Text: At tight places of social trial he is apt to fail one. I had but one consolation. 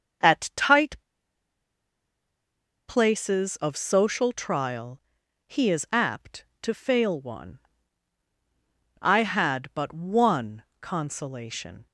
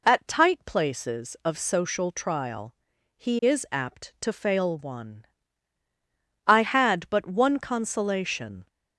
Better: second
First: starts louder than the rest; until 3.1 s; 6.5 dB // pauses between "tight" and "places"; strong; at 0.9 s; 1.9 s long // pauses between "trial" and "he"; noticeable; at 5.0 s; 0.46 s long // pauses between "one" and "consolation"; slight; at 10.6 s; 0.18 s long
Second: pauses between "trial" and "he"; at 2.7 s; 0.42 s long

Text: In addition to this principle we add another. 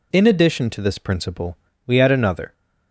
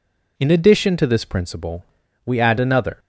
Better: neither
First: pauses between "principle" and "we"; slight; at 1.5 s; 0.30 s long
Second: pauses between "principle" and "we"; at 1.8 s; 0.40 s long

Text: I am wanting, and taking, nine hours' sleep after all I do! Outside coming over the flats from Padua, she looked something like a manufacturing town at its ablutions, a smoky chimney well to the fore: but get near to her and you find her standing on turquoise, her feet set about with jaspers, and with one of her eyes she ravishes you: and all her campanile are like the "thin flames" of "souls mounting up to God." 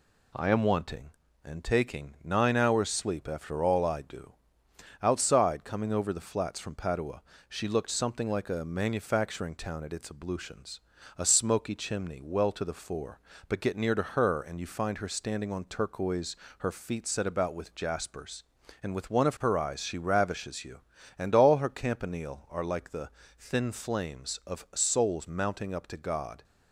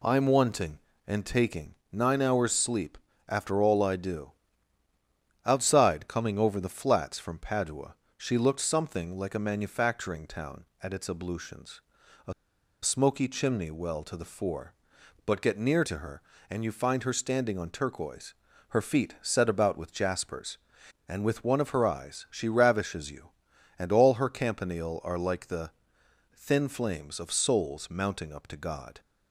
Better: first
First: pauses between "the" and "thin"; slight; at 23.0 s; 0.30 s long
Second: pauses between "sleep" and "after"; slight; at 2.9 s; 0.30 s long // pauses between "a" and "smoky"; noticeable; at 12.3 s; 0.50 s long // pauses between "the" and "thin"; noticeable; at 25.6 s; 0.66 s long

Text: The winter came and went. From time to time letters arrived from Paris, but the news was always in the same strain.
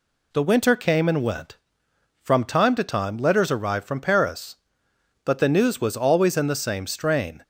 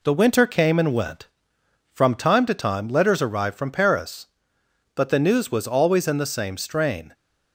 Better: first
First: none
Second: gets quieter; slight; throughout; 3 dB

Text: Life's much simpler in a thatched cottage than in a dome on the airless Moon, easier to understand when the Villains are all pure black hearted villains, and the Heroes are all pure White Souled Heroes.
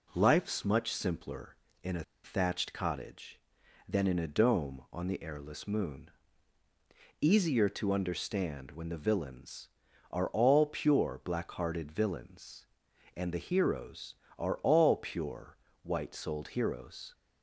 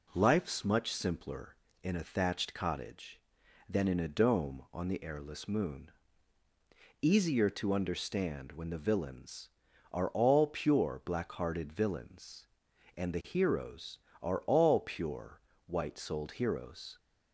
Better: second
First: pauses between "a" and "thatched"; slight; at 2.0 s; 0.21 s long // pauses between "pure" and "White"; slight; at 15.5 s; 0.26 s long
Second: pauses between "pure" and "White"; slight; at 15.3 s; 0.26 s long

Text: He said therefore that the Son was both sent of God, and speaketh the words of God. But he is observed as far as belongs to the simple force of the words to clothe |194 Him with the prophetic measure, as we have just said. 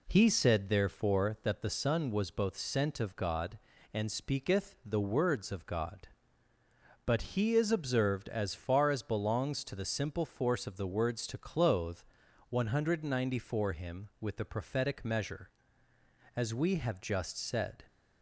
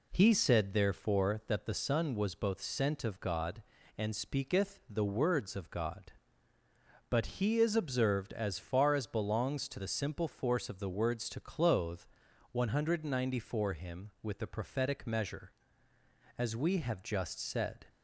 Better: neither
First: none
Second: none

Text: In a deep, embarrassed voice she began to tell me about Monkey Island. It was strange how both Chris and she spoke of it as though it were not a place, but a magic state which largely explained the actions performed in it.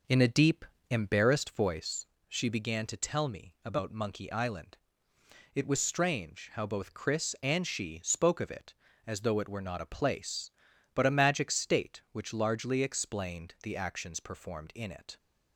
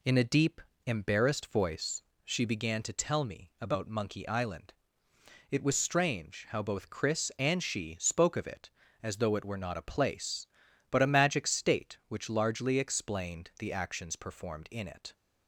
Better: second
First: starts louder than the rest; noticeable; until 1.7 s; 5.5 dB // pauses between "voice" and "she"; slight; at 2.0 s; 0.24 s long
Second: pauses between "voice" and "she"; slight; at 2.0 s; 0.24 s long

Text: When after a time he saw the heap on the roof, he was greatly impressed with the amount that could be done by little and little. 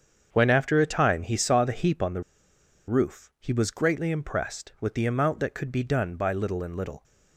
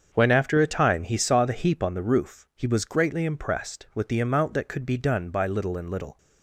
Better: second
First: starts louder than the rest; strong; until 1.3 s; 7.5 dB // pauses between "the" and "roof"; noticeable; at 2.2 s; 0.67 s long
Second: starts louder than the rest; until 1.1 s; 7 dB

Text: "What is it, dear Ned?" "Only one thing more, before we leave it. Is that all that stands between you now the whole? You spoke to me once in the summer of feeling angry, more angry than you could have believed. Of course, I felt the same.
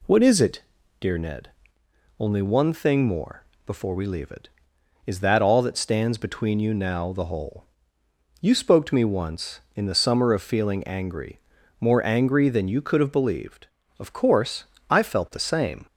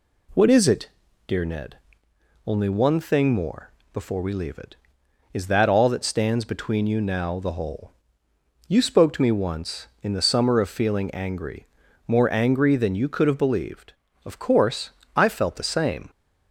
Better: neither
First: none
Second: none

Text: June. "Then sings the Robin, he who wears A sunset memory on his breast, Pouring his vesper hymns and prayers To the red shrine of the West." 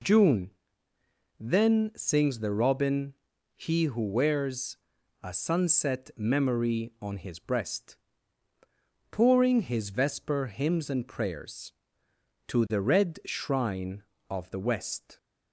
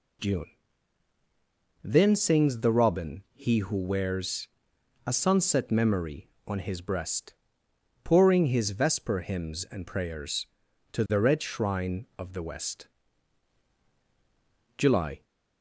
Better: first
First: pauses between "wears" and "A"; noticeable; at 4.7 s; 0.48 s long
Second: pauses between "wears" and "A"; noticeable; at 4.4 s; 0.58 s long // goes on to say "July"; slight; from 14.7 s on; 0.46 s long

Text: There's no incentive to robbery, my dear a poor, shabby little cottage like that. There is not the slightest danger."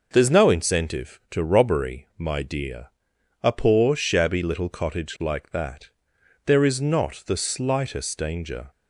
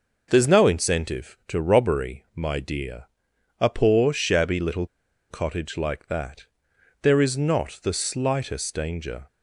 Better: first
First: pauses between "dear" and "a"; noticeable; at 2.8 s; 0.56 s long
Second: pauses between "dear" and "a"; noticeable; at 3.0 s; 0.56 s long // pauses between "little" and "cottage"; at 4.8 s; 0.44 s long

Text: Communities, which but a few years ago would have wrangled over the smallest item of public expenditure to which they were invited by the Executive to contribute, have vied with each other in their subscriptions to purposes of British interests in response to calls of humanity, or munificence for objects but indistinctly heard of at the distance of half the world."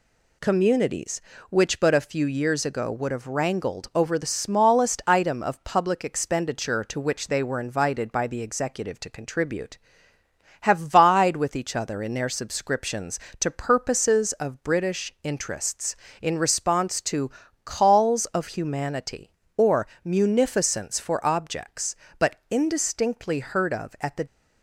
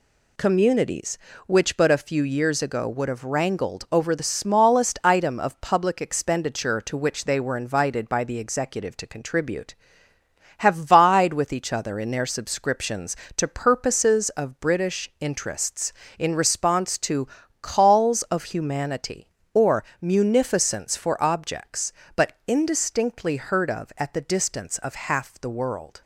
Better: second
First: pauses between "to" and "calls"; slight; at 17.3 s; 0.34 s long // pauses between "or" and "munificence"; slight; at 19.8 s; 0.16 s long // stops before "distance of half the world"; at 24.2 s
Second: pauses between "to" and "calls"; slight; at 17.2 s; 0.34 s long // pauses between "or" and "munificence"; slight; at 19.8 s; 0.16 s long

